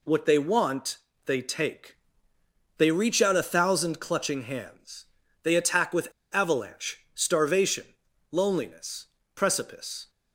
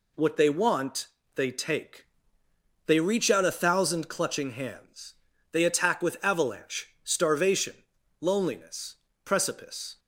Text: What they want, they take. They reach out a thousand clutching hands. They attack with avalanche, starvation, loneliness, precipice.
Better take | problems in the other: second | pauses between "with" and "avalanche"; slight; at 6.1 s; 0.21 s long

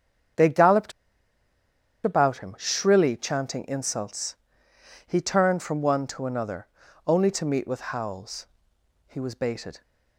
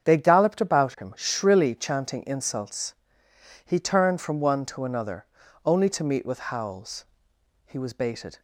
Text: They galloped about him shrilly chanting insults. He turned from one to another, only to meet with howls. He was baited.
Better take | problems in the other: second | starts louder than the rest; strong; until 2.5 s; 7.5 dB; strong in the second // pauses between "galloped" and "about"; at 0.9 s; 1.1 s long

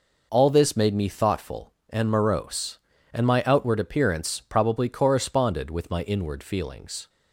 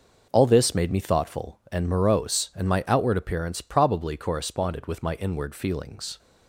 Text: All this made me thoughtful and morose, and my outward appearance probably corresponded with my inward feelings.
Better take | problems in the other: neither | none

